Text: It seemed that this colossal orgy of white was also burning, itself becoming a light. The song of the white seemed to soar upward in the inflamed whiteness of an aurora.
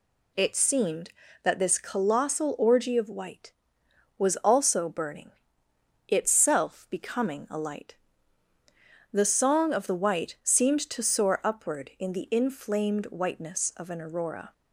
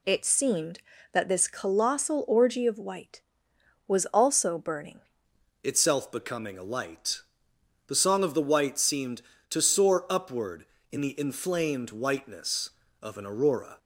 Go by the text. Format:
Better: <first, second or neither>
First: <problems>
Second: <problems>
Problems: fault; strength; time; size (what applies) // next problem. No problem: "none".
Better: first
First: none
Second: changes voice at "itself"; from 5.6 s on; 8.1 s long